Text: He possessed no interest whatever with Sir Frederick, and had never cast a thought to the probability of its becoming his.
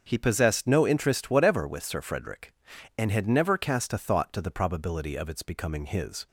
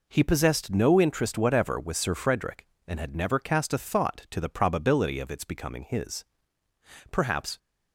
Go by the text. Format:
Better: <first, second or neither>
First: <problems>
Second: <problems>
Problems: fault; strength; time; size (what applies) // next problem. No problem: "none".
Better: first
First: none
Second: goes on to say "Perhaps"; slight; from 7.0 s on; 0.48 s long